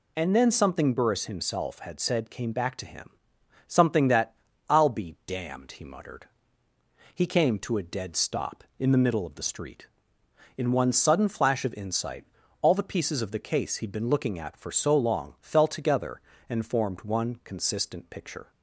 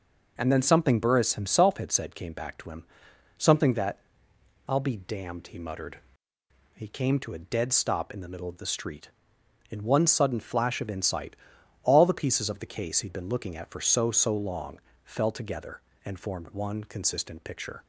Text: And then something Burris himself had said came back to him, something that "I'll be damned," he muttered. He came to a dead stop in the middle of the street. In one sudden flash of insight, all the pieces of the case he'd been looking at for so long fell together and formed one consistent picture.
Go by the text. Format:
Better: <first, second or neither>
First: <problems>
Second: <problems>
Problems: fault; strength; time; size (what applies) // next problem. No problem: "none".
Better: first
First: pauses between "that" and "I'll"; slight; at 4.3 s; 0.34 s long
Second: pauses between "that" and "I'll"; noticeable; at 3.9 s; 0.68 s long // says "so" twice; at 14.0 s // pauses between "long" and "fell"; slight; at 14.7 s; 0.24 s long